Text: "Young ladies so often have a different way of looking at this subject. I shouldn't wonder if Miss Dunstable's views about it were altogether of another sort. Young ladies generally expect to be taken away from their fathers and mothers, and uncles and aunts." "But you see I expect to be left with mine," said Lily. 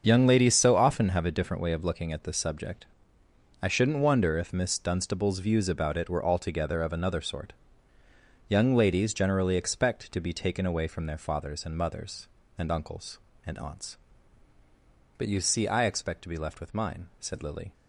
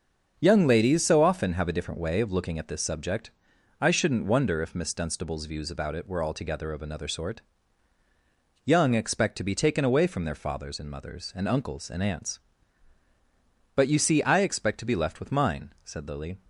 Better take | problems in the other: first | starts louder than the rest; until 1.4 s; 6.5 dB; also in the first // skips "ladies generally"; at 8.9 s

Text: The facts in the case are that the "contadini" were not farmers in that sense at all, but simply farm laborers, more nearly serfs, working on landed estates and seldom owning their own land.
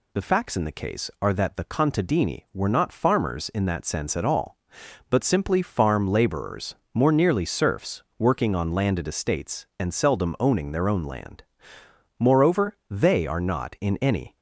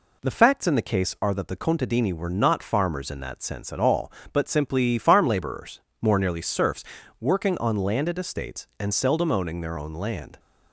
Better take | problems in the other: second | goes on to say "Moreover they are not in any"; strong; from 12.1 s on; 2.1 s long

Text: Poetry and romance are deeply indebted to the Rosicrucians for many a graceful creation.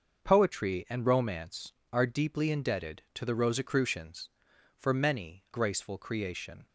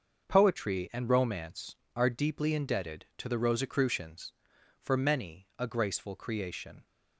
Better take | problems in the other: second | starts louder than the rest; until 1.2 s; 6.5 dB; also in the second // skips "a"; at 5.4 s

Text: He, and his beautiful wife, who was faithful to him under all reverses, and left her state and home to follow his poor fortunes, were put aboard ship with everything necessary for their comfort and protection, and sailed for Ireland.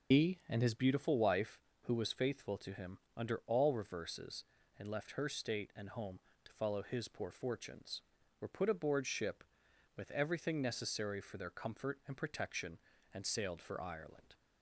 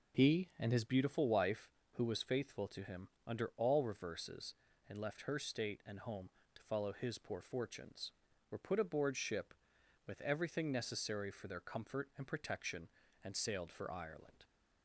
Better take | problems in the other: second | loses the start of "He"; at 0.1 s; 60 ms // pauses between "him" and "under"; slight; at 2.9 s; 0.18 s long; slight in the second

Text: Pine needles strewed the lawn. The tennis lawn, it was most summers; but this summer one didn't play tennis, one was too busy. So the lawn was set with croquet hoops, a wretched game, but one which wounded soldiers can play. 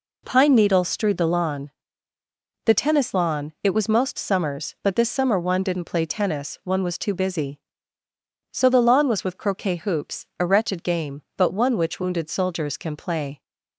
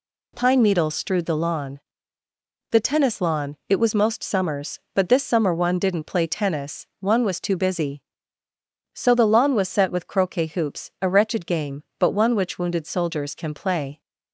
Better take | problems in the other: second | skips "set"; at 9.2 s

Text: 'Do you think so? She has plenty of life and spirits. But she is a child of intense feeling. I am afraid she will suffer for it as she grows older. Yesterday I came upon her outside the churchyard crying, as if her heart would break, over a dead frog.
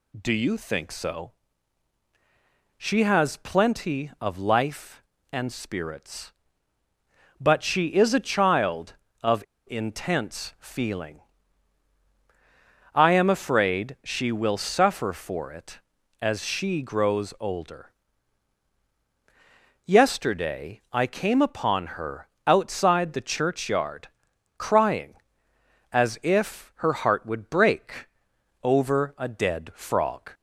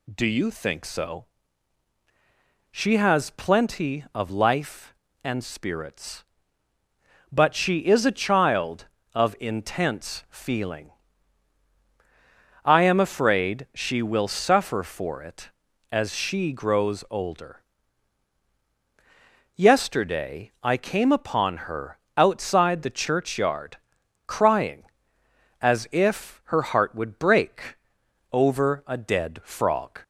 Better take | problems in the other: second | pauses between "of" and "intense"; slight; at 9.4 s; 0.25 s long // pauses between "her" and "outside"; slight; at 22.2 s; 0.18 s long; slight in the second // pauses between "churchyard" and "crying"; noticeable; at 24.0 s; 0.50 s long; noticeable in the second

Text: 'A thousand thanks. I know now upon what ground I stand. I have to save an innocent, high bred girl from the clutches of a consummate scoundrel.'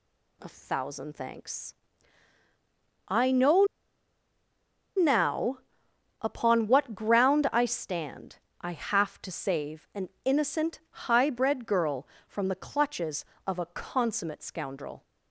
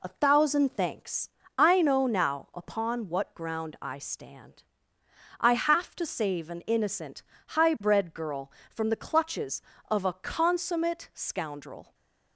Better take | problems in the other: second | pauses between "know" and "now"; strong; at 3.6 s; 1.3 s long // pauses between "now" and "upon"; noticeable; at 5.5 s; 0.64 s long // pauses between "an" and "innocent"; slight; at 10.0 s; 0.16 s long

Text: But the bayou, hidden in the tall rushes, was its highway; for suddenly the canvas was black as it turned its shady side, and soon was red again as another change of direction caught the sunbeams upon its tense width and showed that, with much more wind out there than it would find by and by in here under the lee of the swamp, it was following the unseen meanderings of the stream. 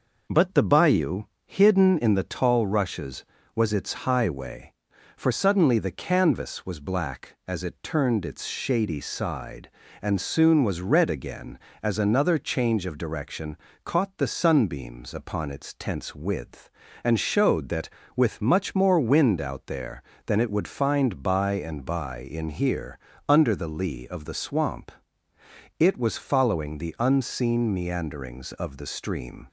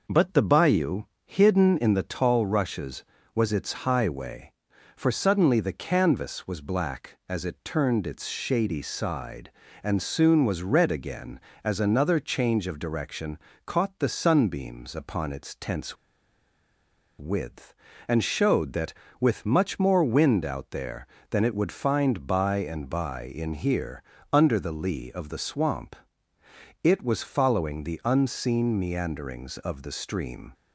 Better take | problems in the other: first | pauses between "direction" and "caught"; slight; at 13.3 s; 0.26 s long; slight in the first // pauses between "tense" and "width"; at 15.9 s; 1.2 s long // pauses between "here" and "under"; slight; at 24.0 s; 0.30 s long; slight in the first

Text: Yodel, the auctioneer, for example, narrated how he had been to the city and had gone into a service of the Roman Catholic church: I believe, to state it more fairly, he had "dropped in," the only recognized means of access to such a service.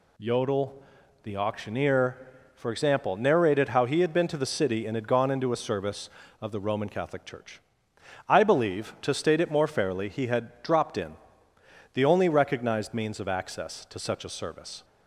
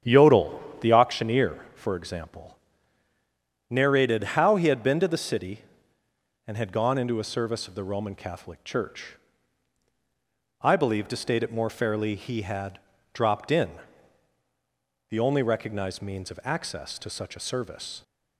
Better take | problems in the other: first | starts louder than the rest; strong; until 1.1 s; 8.5 dB // pauses between "had" and "dropped"; slight; at 12.7 s; 0.34 s long

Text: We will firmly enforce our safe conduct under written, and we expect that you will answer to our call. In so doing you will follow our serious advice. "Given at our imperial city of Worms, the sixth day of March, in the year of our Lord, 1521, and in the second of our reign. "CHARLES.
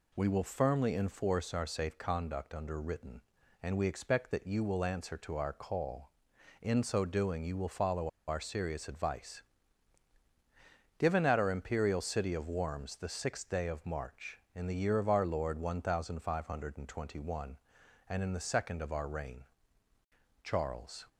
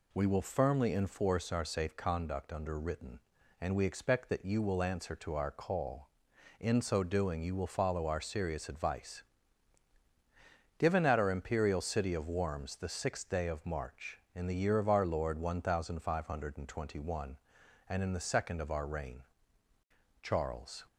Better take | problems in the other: second | pauses between "follow" and "our"; slight; at 8.0 s; 0.19 s long

